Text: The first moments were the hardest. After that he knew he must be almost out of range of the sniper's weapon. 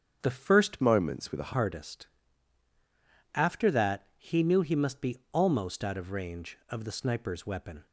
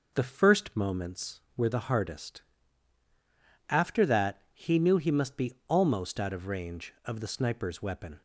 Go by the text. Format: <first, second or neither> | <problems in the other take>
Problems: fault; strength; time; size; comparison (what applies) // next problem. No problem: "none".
second | starts louder than the rest; strong; until 1.2 s; 8 dB // changes voice from "moments" to "the"; from 0.8 to 1.5 s; 0.7 s long